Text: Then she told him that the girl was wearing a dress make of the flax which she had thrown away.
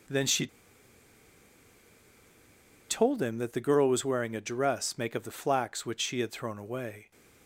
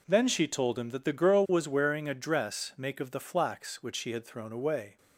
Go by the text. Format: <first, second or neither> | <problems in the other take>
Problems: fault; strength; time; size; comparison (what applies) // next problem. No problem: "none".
second | pauses between "she" and "told"; strong; at 0.4 s; 2.4 s long